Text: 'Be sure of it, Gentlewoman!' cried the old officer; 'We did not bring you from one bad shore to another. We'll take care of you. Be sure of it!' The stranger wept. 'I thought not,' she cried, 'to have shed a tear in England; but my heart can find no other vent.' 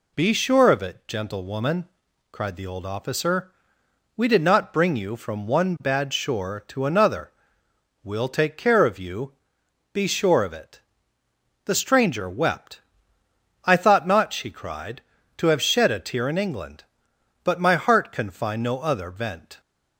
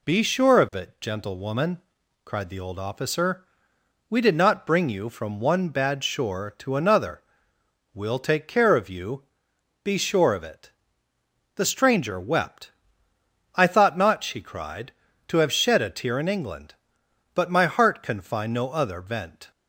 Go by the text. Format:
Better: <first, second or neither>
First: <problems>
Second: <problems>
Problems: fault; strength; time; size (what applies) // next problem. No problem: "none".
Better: neither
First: none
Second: none